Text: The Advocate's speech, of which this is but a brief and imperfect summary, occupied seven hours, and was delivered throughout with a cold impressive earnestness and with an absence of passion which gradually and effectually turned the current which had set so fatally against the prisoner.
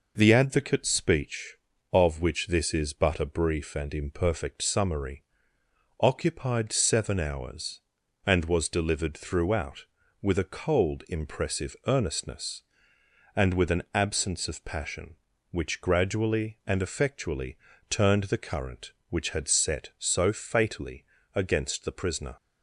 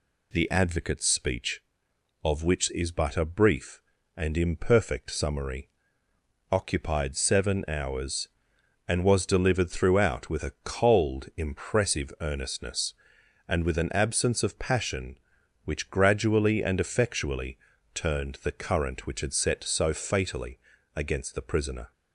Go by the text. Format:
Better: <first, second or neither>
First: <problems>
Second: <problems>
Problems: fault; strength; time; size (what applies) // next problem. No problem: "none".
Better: first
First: pauses between "effectually" and "turned"; slight; at 17.5 s; 0.34 s long // pauses between "fatally" and "against"; slight; at 21.0 s; 0.30 s long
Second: skips "this"; at 2.6 s // pauses between "effectually" and "turned"; at 17.5 s; 0.38 s long // pauses between "fatally" and "against"; at 20.5 s; 0.38 s long